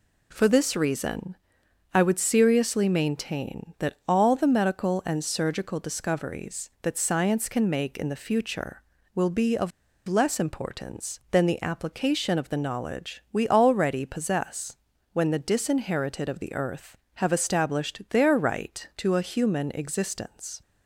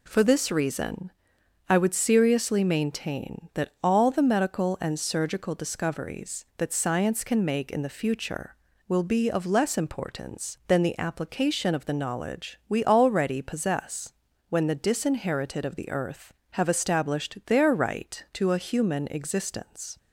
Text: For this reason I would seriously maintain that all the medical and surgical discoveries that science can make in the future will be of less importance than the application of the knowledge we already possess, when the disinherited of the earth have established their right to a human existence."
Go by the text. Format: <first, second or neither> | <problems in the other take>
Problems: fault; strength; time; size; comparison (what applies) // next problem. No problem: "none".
second | pauses between "reason" and "I"; noticeable; at 1.3 s; 0.58 s long; noticeable in the second // pauses between "of" and "less"; at 9.7 s; 0.38 s long